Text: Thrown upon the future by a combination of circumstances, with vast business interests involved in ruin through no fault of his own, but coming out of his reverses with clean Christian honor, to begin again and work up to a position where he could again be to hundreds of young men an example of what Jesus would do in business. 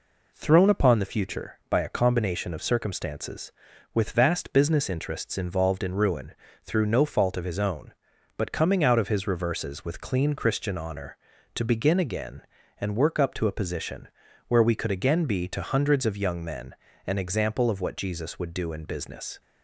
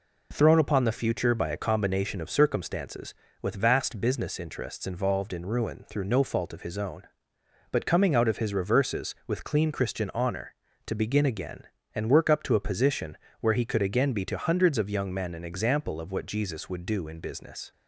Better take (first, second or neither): second